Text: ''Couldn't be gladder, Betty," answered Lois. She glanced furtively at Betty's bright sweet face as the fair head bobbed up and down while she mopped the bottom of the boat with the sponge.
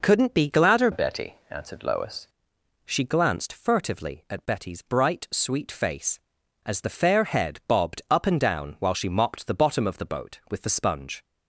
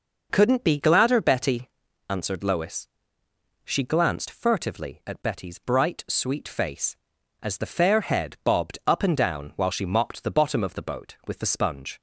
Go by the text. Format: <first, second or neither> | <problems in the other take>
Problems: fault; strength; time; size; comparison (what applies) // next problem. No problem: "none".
second | changes voice from "Betty" to "Lois"; from 0.9 to 2.2 s; 1.3 s long